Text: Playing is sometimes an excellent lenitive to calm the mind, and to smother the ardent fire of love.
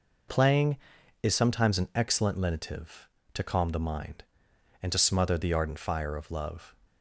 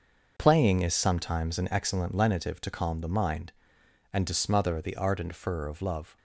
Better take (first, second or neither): first